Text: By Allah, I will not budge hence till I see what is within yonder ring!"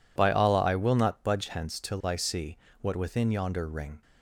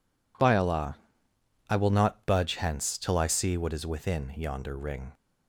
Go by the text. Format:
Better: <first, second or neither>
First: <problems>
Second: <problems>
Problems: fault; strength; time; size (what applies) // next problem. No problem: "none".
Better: second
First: pauses between "see" and "what"; slight; at 2.5 s; 0.24 s long // skips "is"; at 2.9 s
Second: none